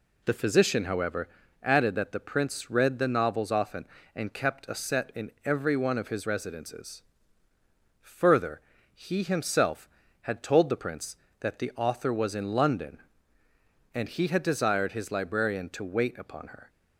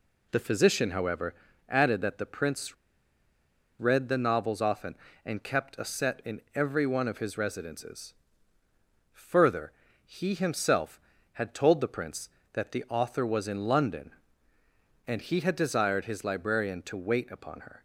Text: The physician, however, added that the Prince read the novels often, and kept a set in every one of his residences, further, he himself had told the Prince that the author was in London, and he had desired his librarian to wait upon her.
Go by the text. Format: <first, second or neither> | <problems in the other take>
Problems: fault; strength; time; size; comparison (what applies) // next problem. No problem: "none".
first | pauses between "Prince" and "read"; at 2.7 s; 1.0 s long